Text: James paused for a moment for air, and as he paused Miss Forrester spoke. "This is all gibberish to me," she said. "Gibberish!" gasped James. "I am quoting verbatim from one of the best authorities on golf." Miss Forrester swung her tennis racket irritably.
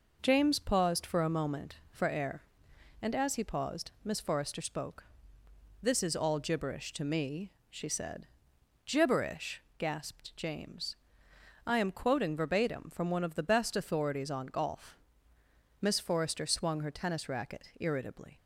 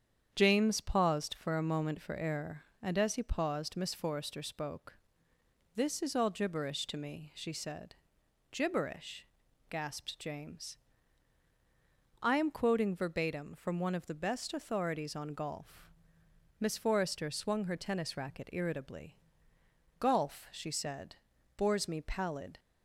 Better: first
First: none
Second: starts louder than the rest; strong; until 1.3 s; 8 dB // goes on to say "Golf she said bores me pallid"; strong; from 19.9 s on; 2.6 s long

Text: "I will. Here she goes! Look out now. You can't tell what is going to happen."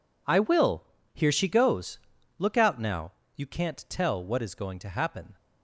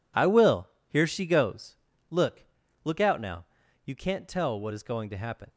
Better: first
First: none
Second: says "Look" twice; at 2.8 s

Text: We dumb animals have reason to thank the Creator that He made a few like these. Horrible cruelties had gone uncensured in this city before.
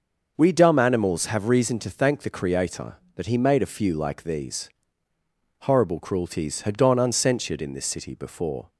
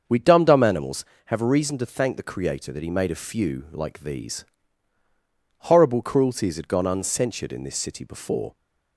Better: first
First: starts louder than the rest; until 1.3 s; 6.5 dB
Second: starts louder than the rest; until 1.3 s; 6.5 dB // says "dumb" twice; at 0.4 s

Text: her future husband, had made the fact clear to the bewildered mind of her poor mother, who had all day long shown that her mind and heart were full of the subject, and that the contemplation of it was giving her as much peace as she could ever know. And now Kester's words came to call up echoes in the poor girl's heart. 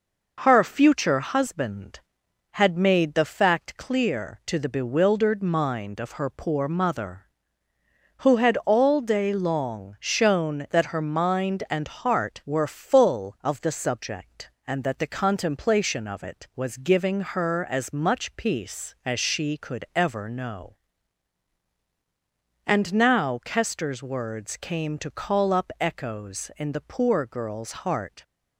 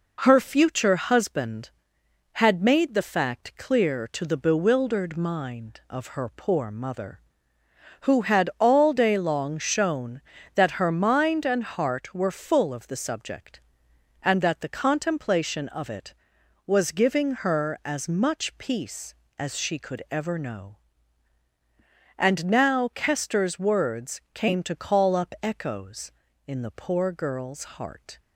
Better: neither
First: none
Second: none

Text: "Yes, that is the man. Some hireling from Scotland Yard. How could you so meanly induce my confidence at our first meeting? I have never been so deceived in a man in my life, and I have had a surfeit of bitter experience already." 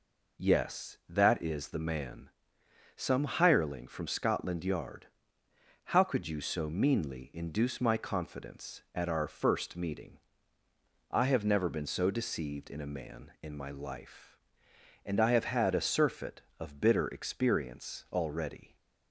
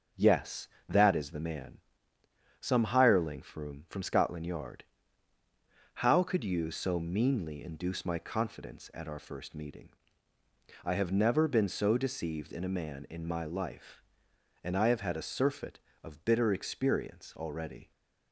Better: first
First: none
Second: starts louder than the rest; until 1.3 s; 6.5 dB // says "from" twice; at 3.8 s

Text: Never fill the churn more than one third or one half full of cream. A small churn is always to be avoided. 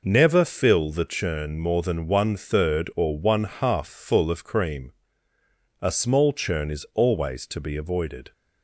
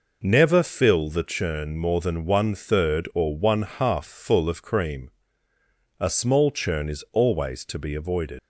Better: first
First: none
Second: leaves "avoided" unfinished; at 8.3 s; 115 ms

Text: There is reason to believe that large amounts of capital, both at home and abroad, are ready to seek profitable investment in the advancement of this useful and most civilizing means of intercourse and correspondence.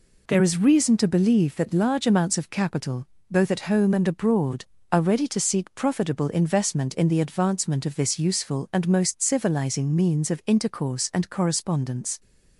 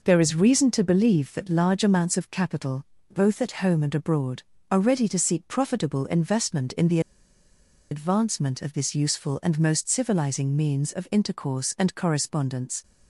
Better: first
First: none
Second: pauses between "the" and "advancement"; noticeable; at 6.9 s; 0.91 s long

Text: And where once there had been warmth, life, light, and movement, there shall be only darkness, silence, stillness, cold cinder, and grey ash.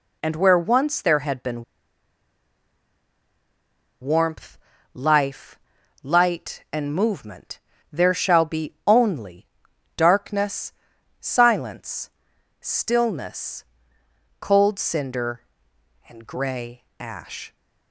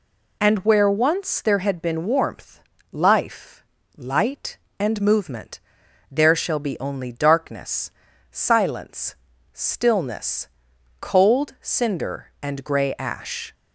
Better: second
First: pauses between "been" and "warmth"; strong; at 1.6 s; 2.3 s long // pauses between "only" and "darkness"; noticeable; at 9.4 s; 0.50 s long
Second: none

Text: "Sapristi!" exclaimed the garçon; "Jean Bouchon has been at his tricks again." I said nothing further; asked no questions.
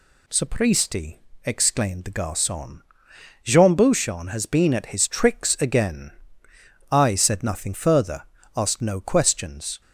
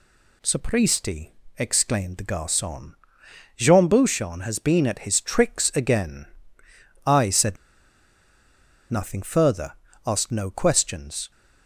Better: first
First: none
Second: pauses between "said" and "nothing"; strong; at 7.5 s; 1.3 s long

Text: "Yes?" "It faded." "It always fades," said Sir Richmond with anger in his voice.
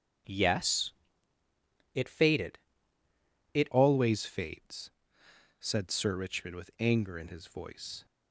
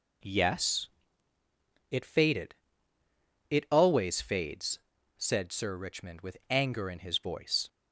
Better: second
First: starts louder than the rest; strong; until 2.3 s; 8.5 dB // changes voice at "always"; from 3.7 s on; 4.3 s long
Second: none

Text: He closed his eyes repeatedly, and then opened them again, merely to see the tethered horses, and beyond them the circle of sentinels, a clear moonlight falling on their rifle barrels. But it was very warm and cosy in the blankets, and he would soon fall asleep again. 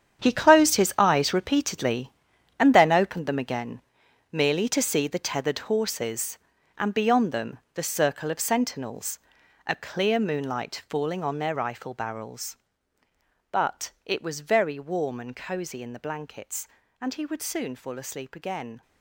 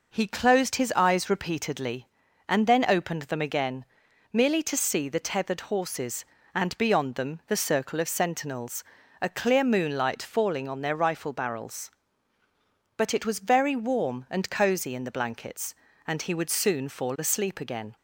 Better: second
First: gets quieter; strong; throughout; 12.5 dB // pauses between "them" and "the"; slight; at 7.5 s; 0.16 s long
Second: none

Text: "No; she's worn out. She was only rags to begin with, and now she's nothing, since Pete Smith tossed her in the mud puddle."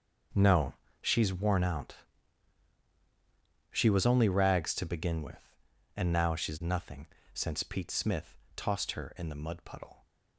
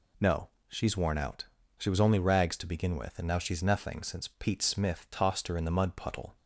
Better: second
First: gets quieter; strong; throughout; 14 dB // pauses between "Smith" and "tossed"; slight; at 8.3 s; 0.20 s long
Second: none

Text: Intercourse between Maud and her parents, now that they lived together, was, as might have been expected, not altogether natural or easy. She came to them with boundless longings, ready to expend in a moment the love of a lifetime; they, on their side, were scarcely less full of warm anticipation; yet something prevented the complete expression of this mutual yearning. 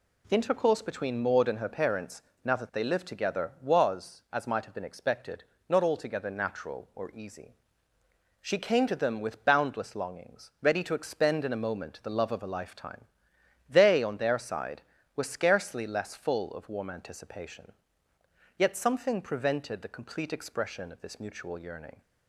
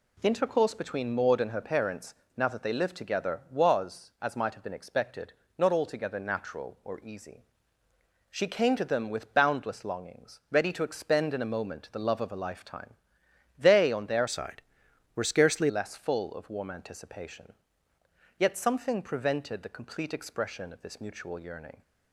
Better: first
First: none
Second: changes voice from "side" to "scarcely"; from 14.2 to 15.6 s; 1.4 s long

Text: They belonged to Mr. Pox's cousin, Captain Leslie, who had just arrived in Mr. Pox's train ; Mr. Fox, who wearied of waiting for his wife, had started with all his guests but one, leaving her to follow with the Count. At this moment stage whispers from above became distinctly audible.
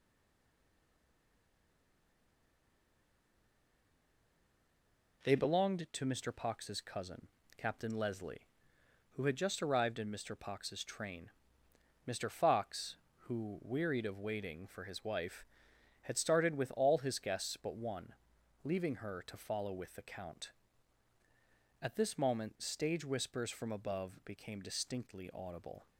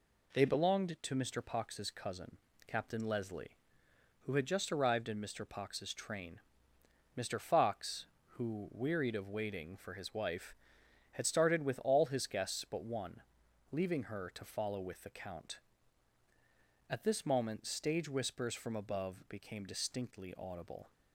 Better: second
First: stays silent before the first word; strong; until 5.2 s; 5.2 s long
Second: none

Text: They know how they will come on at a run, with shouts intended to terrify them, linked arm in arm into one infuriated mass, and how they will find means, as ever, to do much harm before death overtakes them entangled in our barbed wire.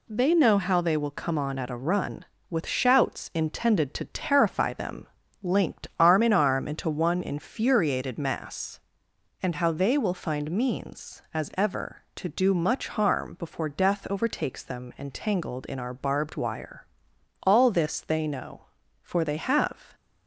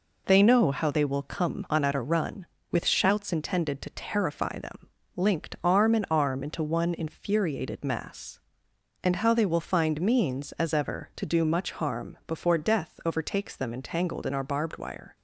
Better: second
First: goes on to say "All this they know for they have"; strong; from 17.4 s on; 2.5 s long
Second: none

